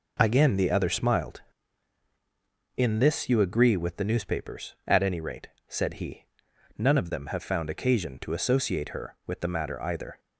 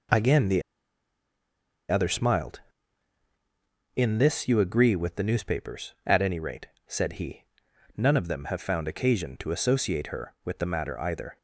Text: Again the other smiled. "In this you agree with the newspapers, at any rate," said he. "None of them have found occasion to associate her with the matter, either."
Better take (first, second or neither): first